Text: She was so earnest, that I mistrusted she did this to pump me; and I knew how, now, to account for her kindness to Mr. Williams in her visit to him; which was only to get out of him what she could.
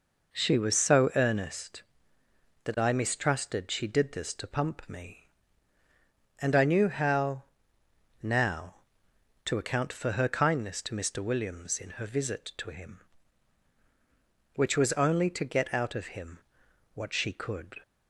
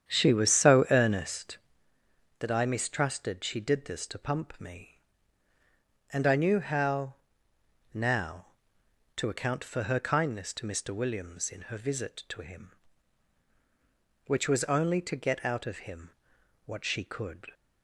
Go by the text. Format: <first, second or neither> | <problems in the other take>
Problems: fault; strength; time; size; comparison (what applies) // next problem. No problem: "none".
first | starts louder than the rest; strong; until 1.8 s; 9 dB // pauses between "him" and "what"; noticeable; at 16.1 s; 0.56 s long; noticeable in the first